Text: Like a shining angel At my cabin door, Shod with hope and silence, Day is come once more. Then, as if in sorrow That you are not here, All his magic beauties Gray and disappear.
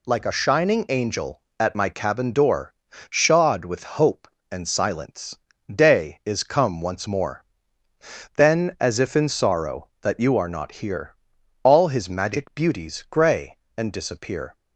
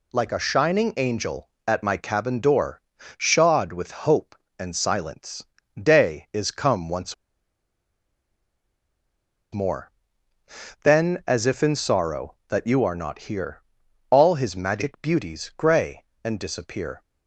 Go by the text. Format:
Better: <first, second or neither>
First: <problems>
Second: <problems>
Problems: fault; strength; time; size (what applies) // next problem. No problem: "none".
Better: first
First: none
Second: pauses between "once" and "more"; strong; at 7.1 s; 2.4 s long